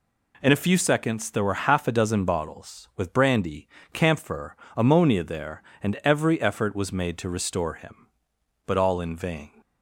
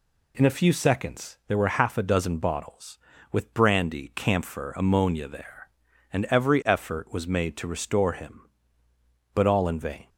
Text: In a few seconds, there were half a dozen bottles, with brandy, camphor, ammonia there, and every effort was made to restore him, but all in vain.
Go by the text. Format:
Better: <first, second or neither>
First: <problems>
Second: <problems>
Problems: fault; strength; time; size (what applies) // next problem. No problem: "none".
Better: neither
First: none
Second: none